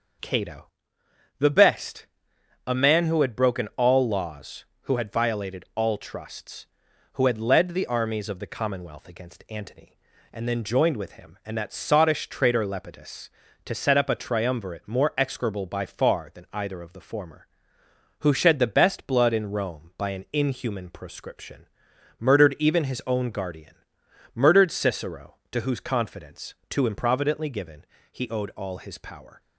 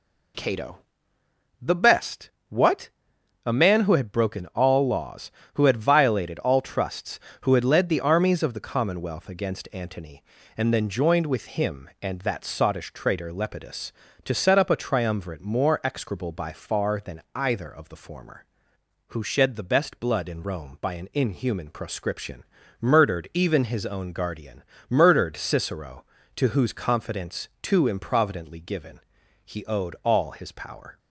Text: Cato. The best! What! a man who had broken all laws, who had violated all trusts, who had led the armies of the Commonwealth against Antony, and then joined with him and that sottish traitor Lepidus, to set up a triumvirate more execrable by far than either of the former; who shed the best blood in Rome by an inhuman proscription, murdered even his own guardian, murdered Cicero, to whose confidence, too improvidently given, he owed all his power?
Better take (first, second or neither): second